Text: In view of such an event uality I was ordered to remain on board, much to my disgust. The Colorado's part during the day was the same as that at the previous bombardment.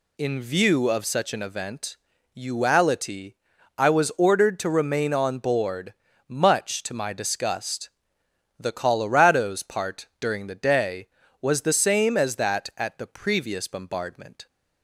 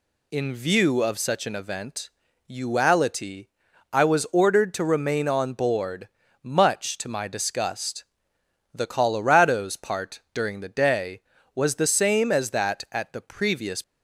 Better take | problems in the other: first | pauses between "event" and "uality"; at 2.0 s; 0.40 s long; also in the first // pauses between "uality" and "I"; noticeable; at 3.4 s; 0.46 s long; also in the first // stops before "bombardment"; at 13.8 s

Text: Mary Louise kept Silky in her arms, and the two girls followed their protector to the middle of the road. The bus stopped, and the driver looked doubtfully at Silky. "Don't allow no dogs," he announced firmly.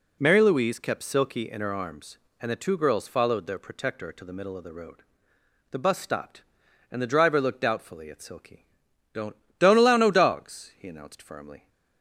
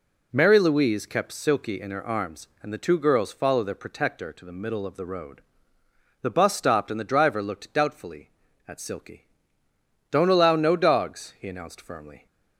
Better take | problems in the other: second | says "Don't" twice; at 9.5 s

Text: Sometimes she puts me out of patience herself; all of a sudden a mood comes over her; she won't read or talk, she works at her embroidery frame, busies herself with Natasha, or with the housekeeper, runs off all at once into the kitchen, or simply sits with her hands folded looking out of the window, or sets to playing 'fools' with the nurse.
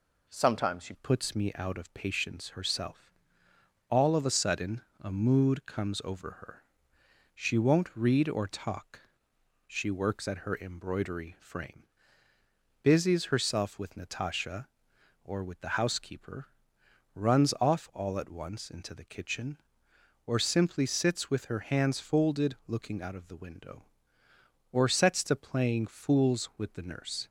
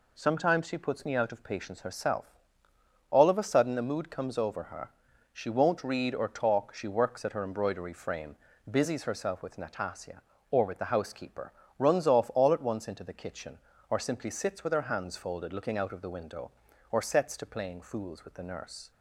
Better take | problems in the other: second | changes voice at "puts"; from 0.9 s on; 26.3 s long // pauses between "sudden" and "a"; slight; at 4.8 s; 0.18 s long

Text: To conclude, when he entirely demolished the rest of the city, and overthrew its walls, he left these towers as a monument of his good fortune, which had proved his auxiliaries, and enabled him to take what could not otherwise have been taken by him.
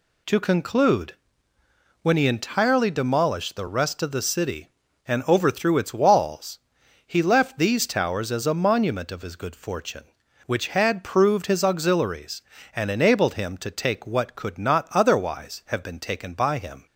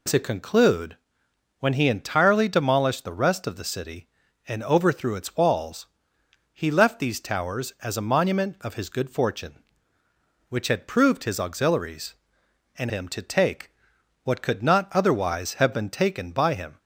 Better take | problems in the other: first | skips "enabled"; at 12.8 s // pauses between "take" and "what"; noticeable; at 13.7 s; 0.50 s long

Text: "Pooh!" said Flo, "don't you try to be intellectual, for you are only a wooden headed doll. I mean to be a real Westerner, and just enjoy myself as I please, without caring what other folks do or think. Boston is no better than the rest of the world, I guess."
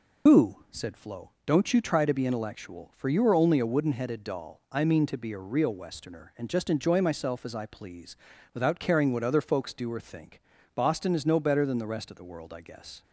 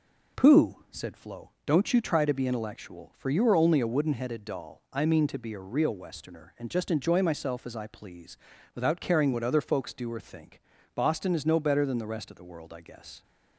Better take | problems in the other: second | loses the start of "Pooh"; at 0.2 s; 95 ms

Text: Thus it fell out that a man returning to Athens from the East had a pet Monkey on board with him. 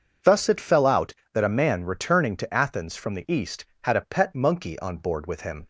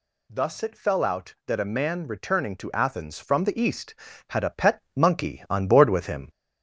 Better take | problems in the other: first | gets louder; slight; throughout; 2.5 dB // pauses between "pet" and "Monkey"; slight; at 4.7 s; 0.16 s long

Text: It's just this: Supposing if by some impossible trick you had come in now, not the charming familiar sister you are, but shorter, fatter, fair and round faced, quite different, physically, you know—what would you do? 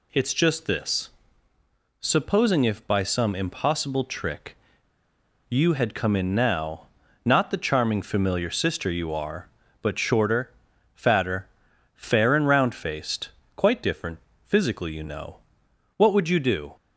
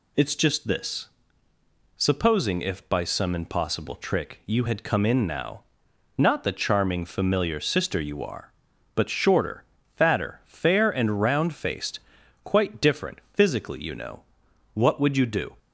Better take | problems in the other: second | pauses between "trick" and "you"; noticeable; at 4.5 s; 0.90 s long

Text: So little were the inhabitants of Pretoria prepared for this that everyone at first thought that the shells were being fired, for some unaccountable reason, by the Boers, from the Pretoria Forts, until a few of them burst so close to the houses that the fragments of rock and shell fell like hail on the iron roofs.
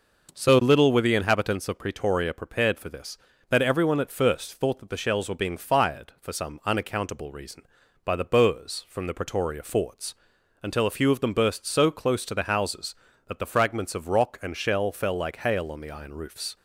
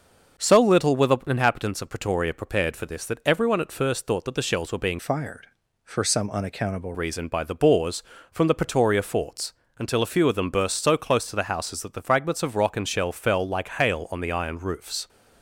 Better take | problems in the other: first | starts louder than the rest; until 1.4 s; 6.5 dB // changes voice from "fired" to "unaccountable"; from 4.9 to 6.9 s; 2.0 s long

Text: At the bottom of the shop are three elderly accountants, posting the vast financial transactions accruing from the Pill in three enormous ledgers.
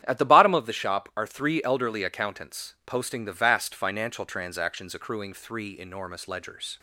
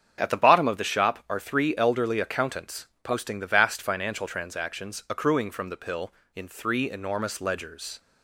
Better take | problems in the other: second | starts louder than the rest; strong; until 1.0 s; 10 dB; strong in the second // skips "from the Pill in"; at 5.3 s

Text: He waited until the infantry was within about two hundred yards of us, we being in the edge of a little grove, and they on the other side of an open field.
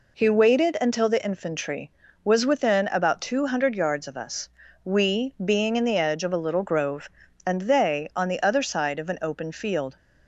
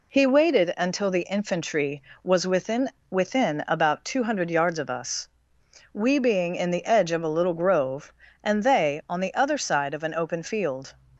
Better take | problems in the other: first | says "within" twice; at 3.1 s

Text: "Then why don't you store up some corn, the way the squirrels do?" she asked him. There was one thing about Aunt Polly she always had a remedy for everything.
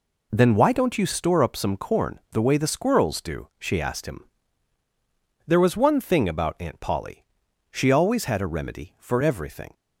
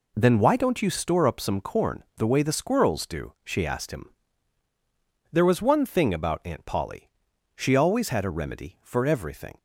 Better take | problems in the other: neither | pauses between "Polly" and "she"; noticeable; the same in both

